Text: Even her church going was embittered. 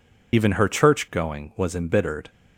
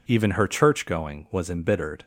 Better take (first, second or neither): second